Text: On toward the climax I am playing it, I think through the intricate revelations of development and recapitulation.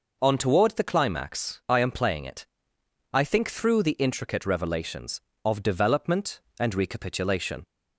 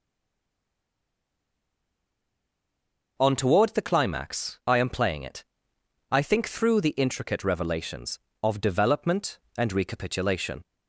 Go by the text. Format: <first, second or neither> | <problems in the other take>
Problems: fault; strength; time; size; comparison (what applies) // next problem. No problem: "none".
first | stays silent before the first word; strong; until 3.1 s; 3.1 s long